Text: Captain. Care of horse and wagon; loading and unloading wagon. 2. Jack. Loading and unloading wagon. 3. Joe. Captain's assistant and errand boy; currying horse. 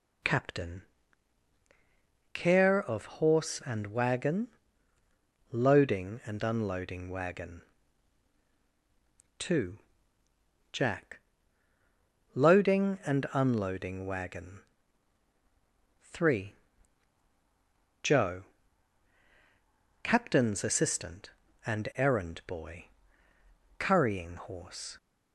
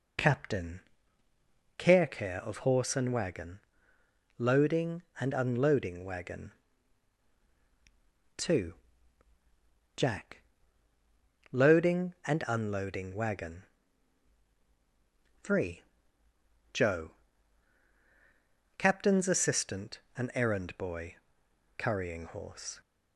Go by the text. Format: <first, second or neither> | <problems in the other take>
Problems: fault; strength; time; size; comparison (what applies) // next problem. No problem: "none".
first | says "Care" twice; at 2.0 s